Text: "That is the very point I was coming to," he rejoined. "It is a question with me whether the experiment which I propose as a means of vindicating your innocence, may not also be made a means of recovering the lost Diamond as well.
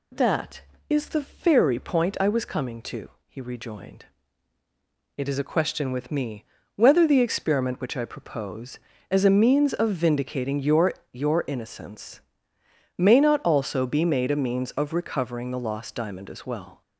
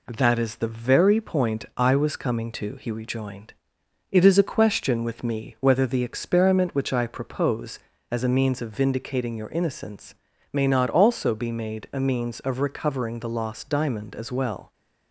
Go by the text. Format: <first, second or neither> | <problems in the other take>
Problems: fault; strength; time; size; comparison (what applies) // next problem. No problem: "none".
second | pauses between "me" and "whether"; slight; at 6.4 s; 0.30 s long // says "your" twice; at 11.1 s